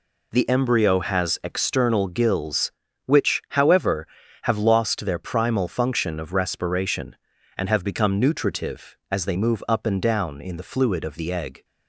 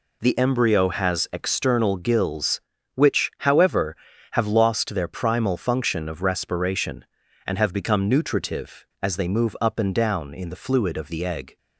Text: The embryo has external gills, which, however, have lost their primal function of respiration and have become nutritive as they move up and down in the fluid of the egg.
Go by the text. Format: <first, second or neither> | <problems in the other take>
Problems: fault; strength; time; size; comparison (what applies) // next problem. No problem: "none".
neither | none